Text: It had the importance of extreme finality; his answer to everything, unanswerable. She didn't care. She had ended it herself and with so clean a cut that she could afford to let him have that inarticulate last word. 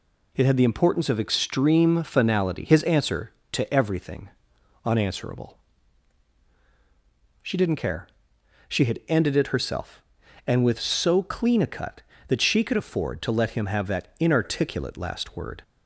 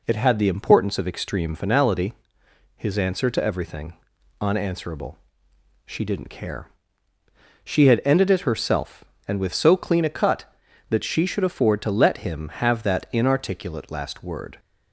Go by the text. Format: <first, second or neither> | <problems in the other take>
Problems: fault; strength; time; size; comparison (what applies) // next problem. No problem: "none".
first | says "should" for "could"; at 11.2 s